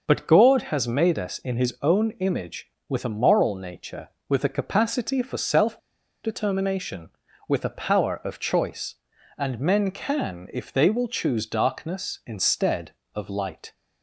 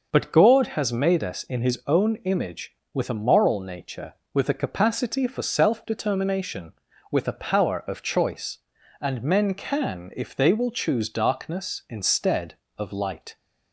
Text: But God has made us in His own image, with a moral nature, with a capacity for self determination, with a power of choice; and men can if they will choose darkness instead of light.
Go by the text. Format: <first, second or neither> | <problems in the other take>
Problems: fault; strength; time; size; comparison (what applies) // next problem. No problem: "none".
second | pauses between "self" and "determination"; noticeable; at 5.7 s; 0.46 s long